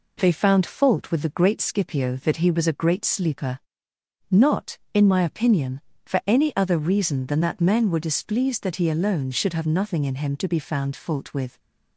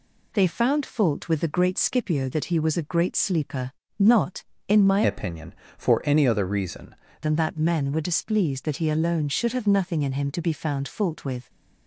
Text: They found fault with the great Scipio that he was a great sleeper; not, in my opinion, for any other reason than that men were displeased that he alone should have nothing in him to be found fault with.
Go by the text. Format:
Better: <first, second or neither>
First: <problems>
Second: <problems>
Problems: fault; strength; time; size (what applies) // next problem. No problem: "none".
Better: first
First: none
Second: changes voice from "opinion" to "reason"; from 5.0 to 6.9 s; 1.9 s long